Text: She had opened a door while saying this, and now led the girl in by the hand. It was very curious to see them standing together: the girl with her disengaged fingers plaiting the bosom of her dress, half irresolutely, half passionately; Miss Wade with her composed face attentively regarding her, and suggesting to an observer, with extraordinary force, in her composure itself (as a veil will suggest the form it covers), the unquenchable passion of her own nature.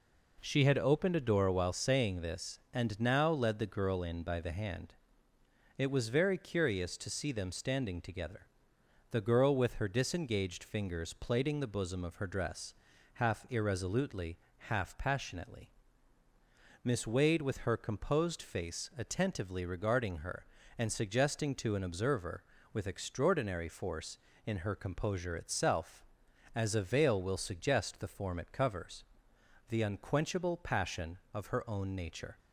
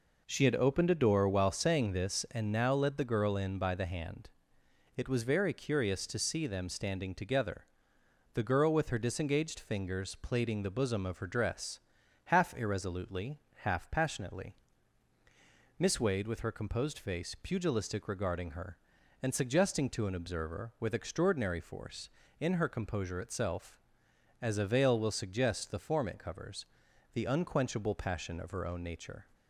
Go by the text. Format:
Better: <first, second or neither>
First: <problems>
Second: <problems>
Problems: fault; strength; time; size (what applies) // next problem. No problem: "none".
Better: first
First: none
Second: says "pugilistic" for "attentively"; at 17.4 s